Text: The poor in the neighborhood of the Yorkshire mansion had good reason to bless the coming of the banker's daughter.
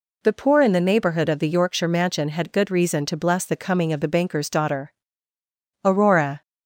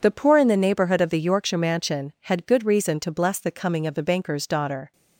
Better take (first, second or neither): second